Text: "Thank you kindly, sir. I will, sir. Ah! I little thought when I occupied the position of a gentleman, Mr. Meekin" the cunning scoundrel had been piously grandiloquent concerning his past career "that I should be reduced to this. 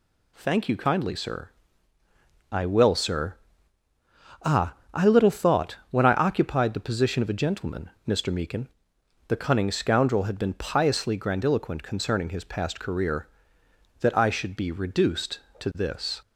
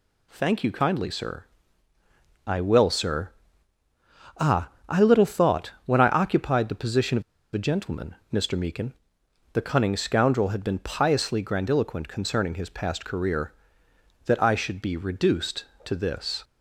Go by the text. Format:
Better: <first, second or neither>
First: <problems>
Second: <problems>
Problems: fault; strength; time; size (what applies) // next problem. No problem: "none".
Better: first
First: pauses between "Meekin" and "the"; noticeable; at 8.6 s; 0.60 s long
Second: pauses between "of" and "a"; slight; at 7.2 s; 0.31 s long // pauses between "Meekin" and "the"; noticeable; at 8.9 s; 0.60 s long